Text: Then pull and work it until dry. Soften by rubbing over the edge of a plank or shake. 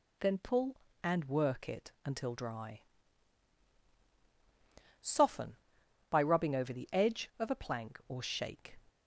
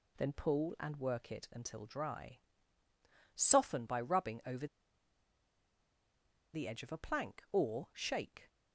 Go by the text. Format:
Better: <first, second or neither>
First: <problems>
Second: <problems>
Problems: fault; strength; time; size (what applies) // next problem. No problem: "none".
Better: first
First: none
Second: pauses between "over" and "the"; strong; at 4.6 s; 1.8 s long